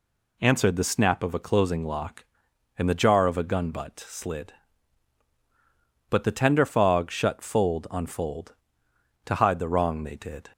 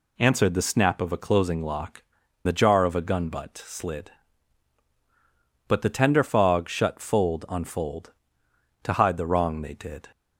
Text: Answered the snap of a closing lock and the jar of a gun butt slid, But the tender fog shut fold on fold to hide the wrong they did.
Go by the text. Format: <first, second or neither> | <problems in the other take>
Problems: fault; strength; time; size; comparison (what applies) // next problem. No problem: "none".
first | skips "and"; at 2.2 s